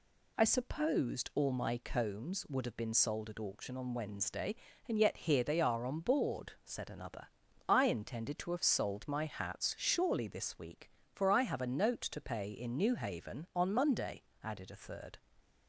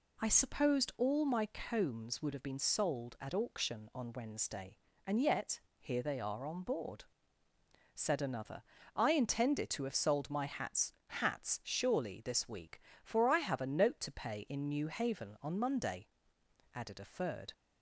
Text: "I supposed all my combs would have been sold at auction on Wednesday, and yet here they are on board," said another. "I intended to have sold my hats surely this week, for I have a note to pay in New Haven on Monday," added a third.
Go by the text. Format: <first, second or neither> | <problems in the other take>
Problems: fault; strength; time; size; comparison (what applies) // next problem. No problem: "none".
first | pauses between "yet" and "here"; slight; at 5.6 s; 0.18 s long // says "hats" twice; at 11.0 s